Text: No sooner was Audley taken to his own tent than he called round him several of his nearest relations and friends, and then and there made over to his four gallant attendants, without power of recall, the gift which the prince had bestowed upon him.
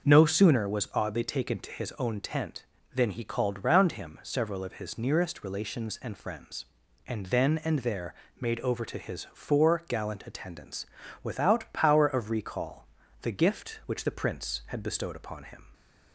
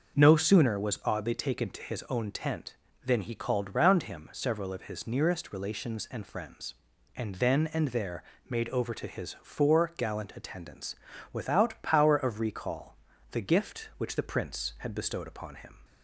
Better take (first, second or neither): neither